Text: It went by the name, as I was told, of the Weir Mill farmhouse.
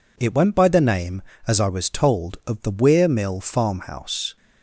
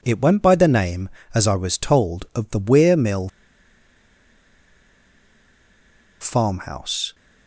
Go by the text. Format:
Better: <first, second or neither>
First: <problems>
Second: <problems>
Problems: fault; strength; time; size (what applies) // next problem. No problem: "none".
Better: first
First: none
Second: pauses between "Mill" and "farmhouse"; strong; at 3.2 s; 2.9 s long